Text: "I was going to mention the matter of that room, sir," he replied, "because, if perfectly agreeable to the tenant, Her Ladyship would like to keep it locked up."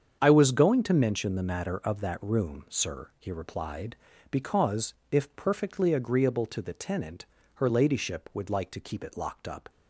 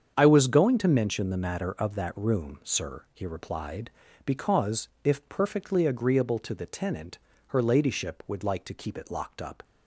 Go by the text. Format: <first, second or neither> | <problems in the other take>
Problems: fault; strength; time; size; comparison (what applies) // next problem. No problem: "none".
neither | starts louder than the rest; strong; the same in both